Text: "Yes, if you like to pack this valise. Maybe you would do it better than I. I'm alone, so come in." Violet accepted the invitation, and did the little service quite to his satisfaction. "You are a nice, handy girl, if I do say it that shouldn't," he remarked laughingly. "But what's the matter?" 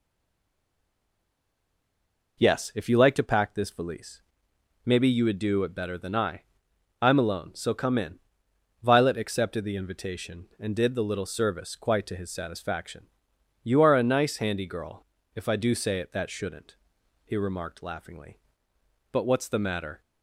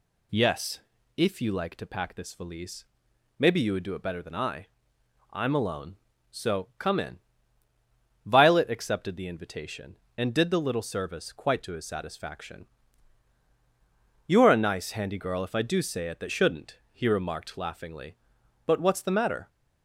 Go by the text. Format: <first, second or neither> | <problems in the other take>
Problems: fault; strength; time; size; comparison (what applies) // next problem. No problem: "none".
second | stays silent before the first word; until 2.3 s; 2.3 s long